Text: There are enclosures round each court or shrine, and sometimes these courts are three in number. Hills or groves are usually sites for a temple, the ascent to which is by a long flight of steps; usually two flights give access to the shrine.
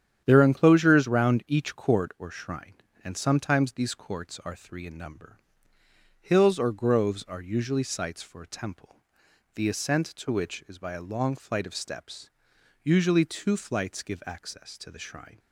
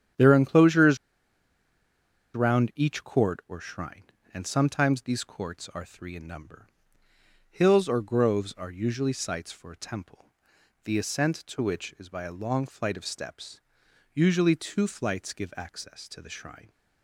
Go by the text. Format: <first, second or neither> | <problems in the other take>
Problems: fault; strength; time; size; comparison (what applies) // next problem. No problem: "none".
first | starts louder than the rest; strong; until 2.5 s; 9.5 dB; strong in the first // pauses between "enclosures" and "round"; strong; at 0.9 s; 1.3 s long